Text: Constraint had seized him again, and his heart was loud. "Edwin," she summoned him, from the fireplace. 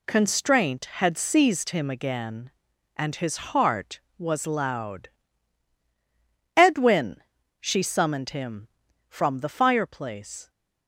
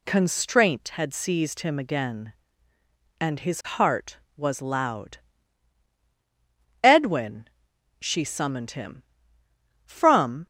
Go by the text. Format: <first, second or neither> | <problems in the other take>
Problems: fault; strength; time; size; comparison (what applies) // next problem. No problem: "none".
first | stops before "the fireplace"; at 10.4 s